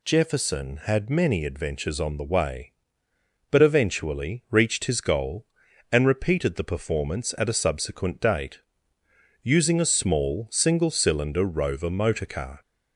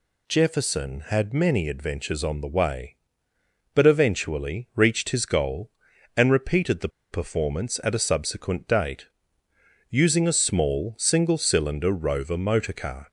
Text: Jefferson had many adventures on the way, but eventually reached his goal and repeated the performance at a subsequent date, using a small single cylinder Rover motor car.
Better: first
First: none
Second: pauses between "the" and "performance"; slight; at 6.8 s; 0.22 s long

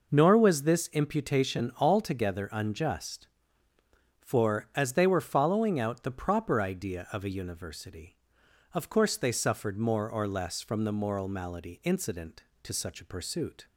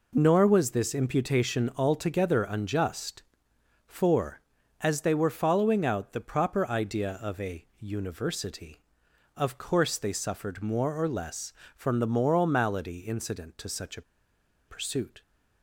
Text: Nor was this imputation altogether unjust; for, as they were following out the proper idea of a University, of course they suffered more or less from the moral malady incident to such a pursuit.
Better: first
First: none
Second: pauses between "a" and "pursuit"; noticeable; at 14.0 s; 0.66 s long

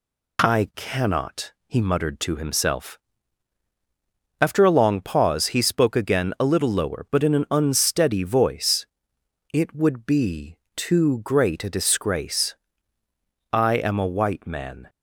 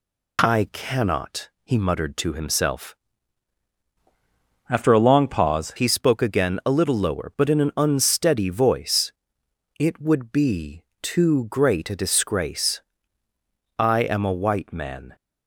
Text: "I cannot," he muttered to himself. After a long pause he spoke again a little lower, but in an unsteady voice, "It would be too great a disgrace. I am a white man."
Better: first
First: pauses between "be" and "too"; slight; at 10.5 s; 0.18 s long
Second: changes voice from "After" to "pause"; from 4.6 to 5.7 s; 1.1 s long // pauses between "be" and "too"; slight; at 10.8 s; 0.18 s long

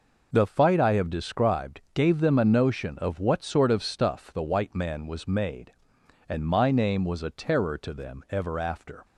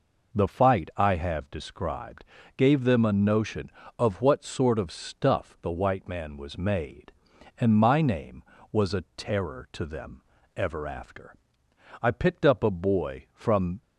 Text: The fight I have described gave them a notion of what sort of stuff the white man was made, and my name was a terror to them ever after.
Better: first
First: none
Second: pauses between "described" and "gave"; slight; at 2.2 s; 0.32 s long // pauses between "them" and "ever"; slight; at 10.2 s; 0.34 s long // goes on to say "I picked up a boy from"; strong; from 12.0 s on; 1.8 s long

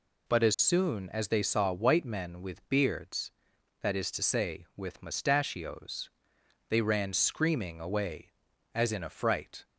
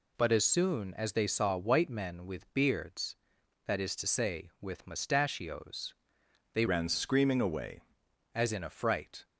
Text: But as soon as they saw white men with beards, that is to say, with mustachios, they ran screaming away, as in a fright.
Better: first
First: none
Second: changes voice from "ran" to "away"; from 6.6 to 7.8 s; 1.2 s long

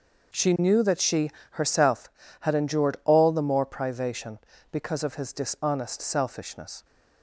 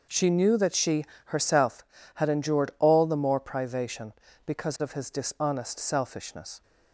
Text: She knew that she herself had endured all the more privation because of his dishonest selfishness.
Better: neither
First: pauses between "she" and "herself"; slight; at 1.3 s; 0.22 s long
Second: pauses between "she" and "herself"; slight; at 1.0 s; 0.22 s long

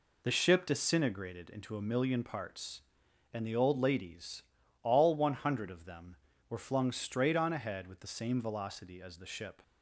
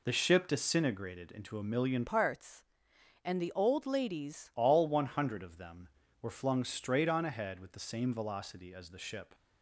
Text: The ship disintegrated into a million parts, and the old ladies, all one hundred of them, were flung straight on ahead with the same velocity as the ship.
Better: first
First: none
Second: changes voice from "parts" to "ladies"; from 2.0 to 4.5 s; 2.5 s long

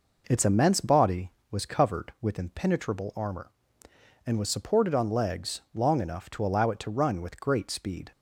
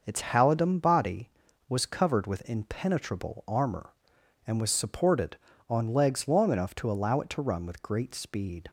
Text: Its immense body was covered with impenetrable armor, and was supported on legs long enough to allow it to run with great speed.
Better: first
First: none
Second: says "halidom" for "immense"; at 0.2 s

